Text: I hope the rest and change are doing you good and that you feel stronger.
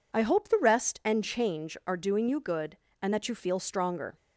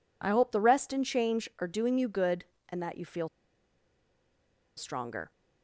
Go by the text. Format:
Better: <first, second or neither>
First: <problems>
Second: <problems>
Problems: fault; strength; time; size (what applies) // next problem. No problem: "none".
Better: first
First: none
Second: pauses between "feel" and "stronger"; strong; at 3.2 s; 1.4 s long